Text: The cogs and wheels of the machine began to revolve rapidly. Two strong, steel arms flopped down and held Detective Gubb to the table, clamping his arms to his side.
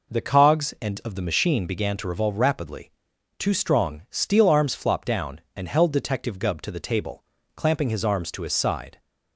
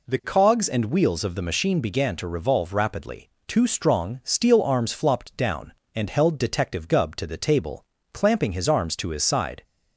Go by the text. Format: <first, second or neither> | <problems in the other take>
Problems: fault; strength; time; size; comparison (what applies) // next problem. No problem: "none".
second | skips "wheels"; at 1.0 s